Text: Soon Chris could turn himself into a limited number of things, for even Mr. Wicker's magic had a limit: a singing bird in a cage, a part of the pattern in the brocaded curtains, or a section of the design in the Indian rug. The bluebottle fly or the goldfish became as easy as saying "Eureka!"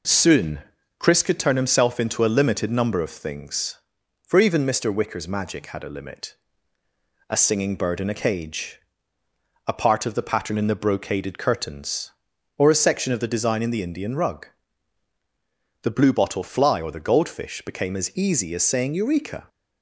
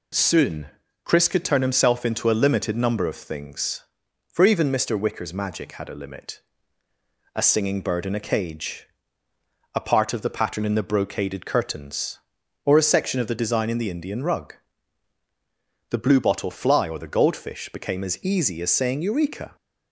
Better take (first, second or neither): second